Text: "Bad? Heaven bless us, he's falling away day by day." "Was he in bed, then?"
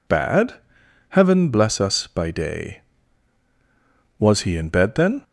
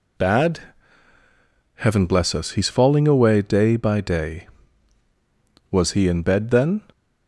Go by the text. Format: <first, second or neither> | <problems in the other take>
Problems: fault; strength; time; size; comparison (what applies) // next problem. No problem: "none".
second | skips "he's falling away day"; at 2.0 s